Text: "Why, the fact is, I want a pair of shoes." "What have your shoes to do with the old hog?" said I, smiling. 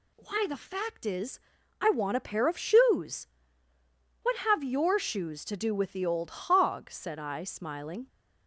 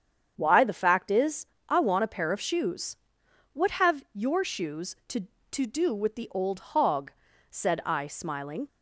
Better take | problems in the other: first | starts louder than the rest; strong; until 1.3 s; 8 dB // says "to" twice; at 5.5 s

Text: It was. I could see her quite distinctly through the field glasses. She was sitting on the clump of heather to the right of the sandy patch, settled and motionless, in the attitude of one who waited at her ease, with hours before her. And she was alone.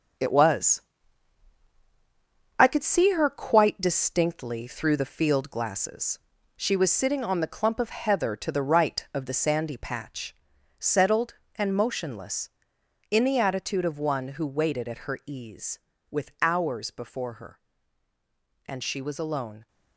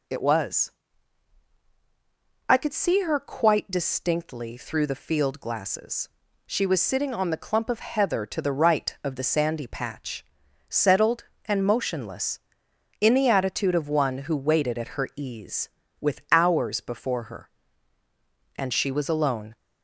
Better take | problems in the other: second | gets quieter; strong; throughout; 8 dB

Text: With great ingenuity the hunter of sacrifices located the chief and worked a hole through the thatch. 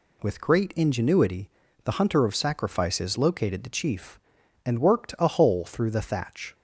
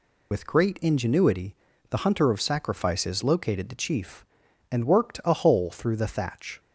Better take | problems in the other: first | loses the start of "With"; at 0.3 s; 45 ms // pauses between "ingenuity" and "the"; slight; at 1.5 s; 0.36 s long; slight in the first

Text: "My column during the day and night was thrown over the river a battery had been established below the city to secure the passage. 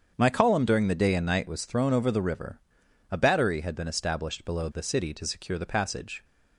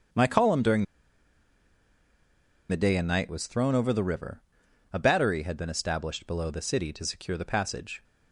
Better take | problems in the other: first | starts louder than the rest; strong; until 3.0 s; 7.5 dB; strong in the first // pauses between "during" and "the"; strong; at 0.8 s; 1.8 s long // pauses between "river" and "a"; noticeable; at 4.4 s; 0.50 s long; noticeable in the first

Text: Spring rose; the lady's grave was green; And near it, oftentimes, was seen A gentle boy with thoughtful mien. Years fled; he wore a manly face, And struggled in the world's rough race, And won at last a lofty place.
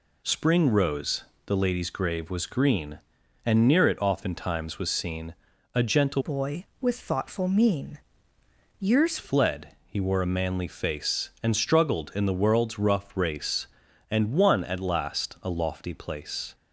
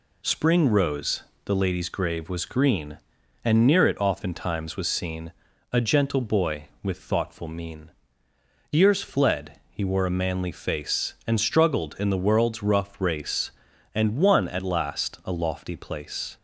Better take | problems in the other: second | pauses between "seen" and "A"; at 5.3 s; 0.40 s long; also in the second // changes voice from "boy" to "Years"; from 6.2 to 9.1 s; 2.9 s long

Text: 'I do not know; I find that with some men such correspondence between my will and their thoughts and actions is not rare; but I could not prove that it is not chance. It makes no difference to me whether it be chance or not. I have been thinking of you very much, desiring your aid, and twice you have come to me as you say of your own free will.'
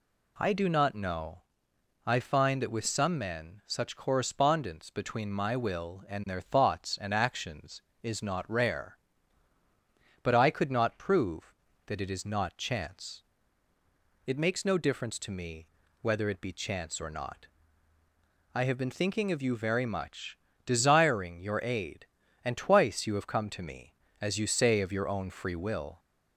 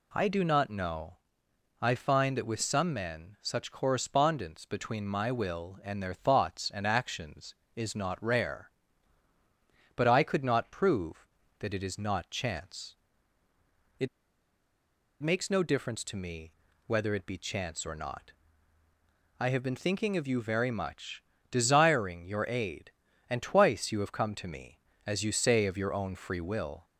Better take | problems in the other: first | pauses between "It" and "makes"; at 14.0 s; 1.1 s long // pauses between "me" and "whether"; slight; at 16.5 s; 0.34 s long; slight in the first

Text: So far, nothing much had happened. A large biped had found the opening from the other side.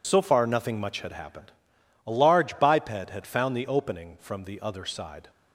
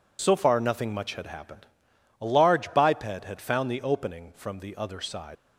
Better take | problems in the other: first | leaves "side" unfinished; at 5.3 s; 100 ms

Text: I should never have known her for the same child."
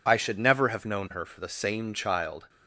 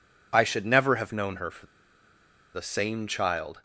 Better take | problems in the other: first | pauses between "for" and "the"; noticeable; at 1.6 s; 0.88 s long

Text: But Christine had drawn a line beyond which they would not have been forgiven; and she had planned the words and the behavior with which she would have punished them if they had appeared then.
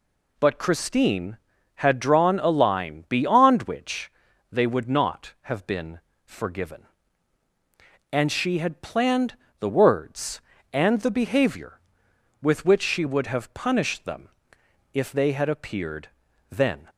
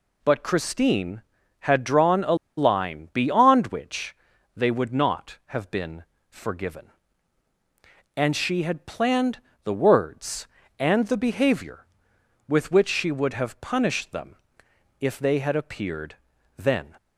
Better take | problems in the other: first | pauses between "a" and "line"; slight; at 2.3 s; 0.22 s long // pauses between "which" and "they"; at 4.1 s; 0.42 s long; also in the first // pauses between "been" and "forgiven"; slight; at 6.0 s; 0.26 s long; slight in the first // pauses between "planned" and "the"; slight; at 9.4 s; 0.24 s long; slight in the first // pauses between "them" and "if"; noticeable; at 14.3 s; 0.64 s long; noticeable in the first // pauses between "appeared" and "then"; at 16.1 s; 0.42 s long; also in the first

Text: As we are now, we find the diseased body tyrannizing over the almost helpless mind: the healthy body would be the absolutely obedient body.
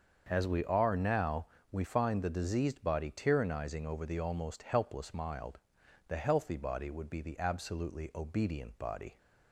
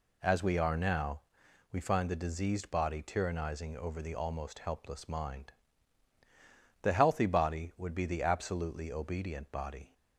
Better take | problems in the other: second | starts louder than the rest; until 1.2 s; 6.5 dB // says "mild" for "mind"; at 5.1 s

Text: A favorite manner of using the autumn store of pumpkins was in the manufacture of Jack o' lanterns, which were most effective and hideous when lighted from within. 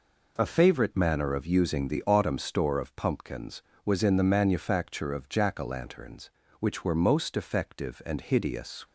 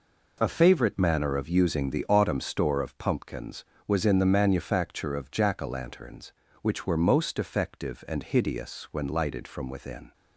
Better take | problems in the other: second | stops before "when lighted from within"; at 8.8 s

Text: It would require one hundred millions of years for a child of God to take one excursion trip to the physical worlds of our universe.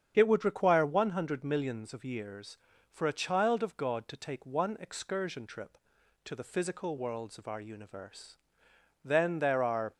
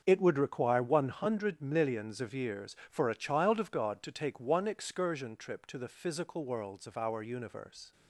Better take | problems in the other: second | starts louder than the rest; strong; until 1.1 s; 8 dB; also in the second // goes on to say "Then there are"; noticeable; from 9.0 s on; 0.90 s long

